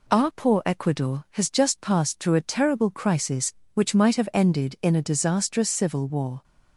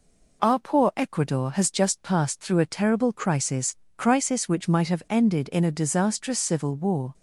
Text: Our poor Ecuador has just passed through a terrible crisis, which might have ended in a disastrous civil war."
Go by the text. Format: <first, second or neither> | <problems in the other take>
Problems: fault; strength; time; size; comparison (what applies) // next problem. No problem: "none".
first | says "crisis" twice; at 3.9 s